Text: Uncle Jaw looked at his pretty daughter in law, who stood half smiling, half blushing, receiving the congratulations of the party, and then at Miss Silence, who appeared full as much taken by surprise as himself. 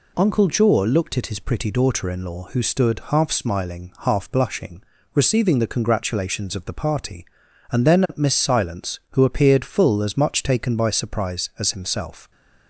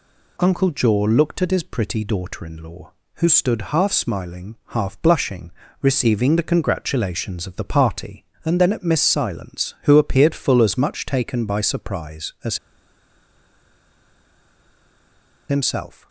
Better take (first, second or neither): first